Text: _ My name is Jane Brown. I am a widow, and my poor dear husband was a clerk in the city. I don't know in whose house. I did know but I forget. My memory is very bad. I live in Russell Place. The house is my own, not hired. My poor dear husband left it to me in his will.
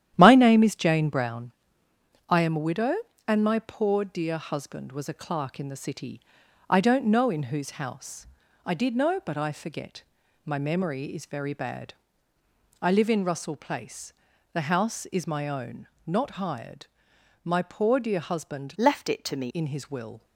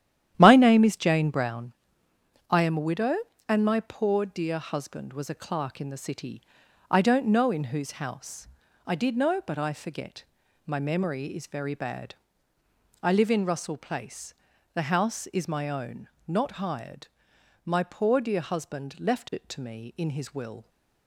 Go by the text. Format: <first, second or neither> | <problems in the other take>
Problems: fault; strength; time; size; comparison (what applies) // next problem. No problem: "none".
second | starts louder than the rest; strong; until 1.1 s; 11 dB; strong in the second // changes voice from "left" to "me"; from 18.7 to 19.4 s; 0.7 s long